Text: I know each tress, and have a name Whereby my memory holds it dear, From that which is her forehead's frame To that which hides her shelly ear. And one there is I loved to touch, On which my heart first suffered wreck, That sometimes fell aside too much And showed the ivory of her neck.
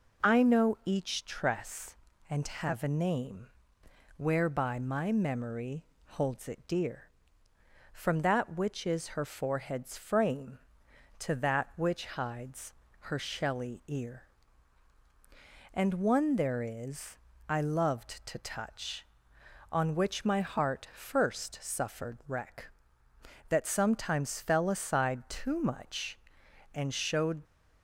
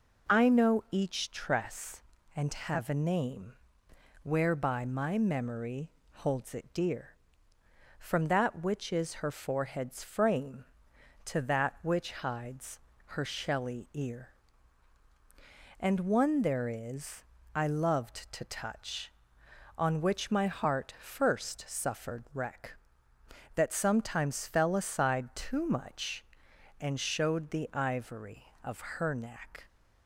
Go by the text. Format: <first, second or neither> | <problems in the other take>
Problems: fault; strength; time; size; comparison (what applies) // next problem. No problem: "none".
second | pauses between "name" and "Whereby"; noticeable; at 3.4 s; 0.70 s long; noticeable in the second // pauses between "memory" and "holds"; slight; at 5.8 s; 0.26 s long; slight in the second // pauses between "hides" and "her"; slight; at 12.7 s; 0.32 s long; slight in the second // pauses between "is" and "I"; slight; at 17.1 s; 0.32 s long; slight in the second // stops before "the ivory of her neck"; at 27.4 s